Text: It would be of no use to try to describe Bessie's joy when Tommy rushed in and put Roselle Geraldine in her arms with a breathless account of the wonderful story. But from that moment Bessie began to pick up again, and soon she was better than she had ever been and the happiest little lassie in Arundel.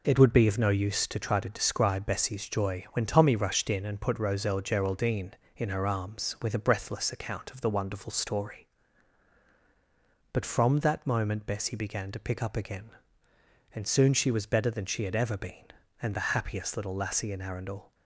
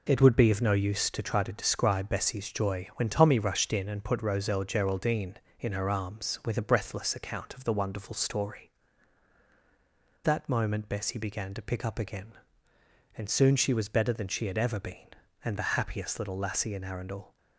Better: first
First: none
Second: skips "But from"; at 9.4 s

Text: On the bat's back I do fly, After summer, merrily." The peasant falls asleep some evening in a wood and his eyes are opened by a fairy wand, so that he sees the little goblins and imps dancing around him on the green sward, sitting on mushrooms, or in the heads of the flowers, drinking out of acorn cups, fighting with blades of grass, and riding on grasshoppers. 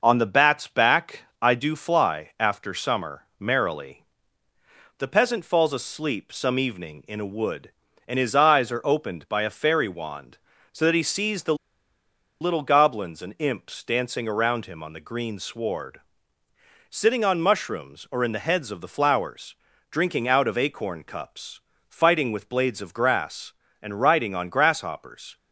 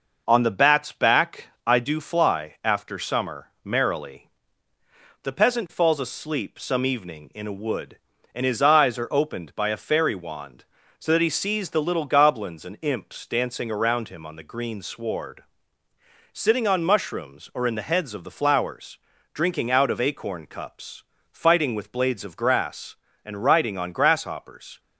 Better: second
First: pauses between "back" and "I"; slight; at 1.2 s; 0.18 s long // pauses between "the" and "little"; noticeable; at 11.5 s; 0.86 s long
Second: pauses between "back" and "I"; slight; at 1.4 s; 0.18 s long

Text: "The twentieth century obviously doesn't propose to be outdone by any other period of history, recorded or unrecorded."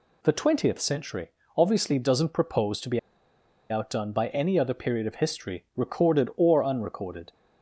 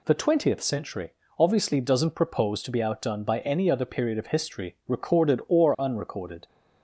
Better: second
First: pauses between "century" and "obviously"; slight; at 1.3 s; 0.26 s long // pauses between "be" and "outdone"; noticeable; at 2.9 s; 0.71 s long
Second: pauses between "century" and "obviously"; slight; at 1.1 s; 0.26 s long

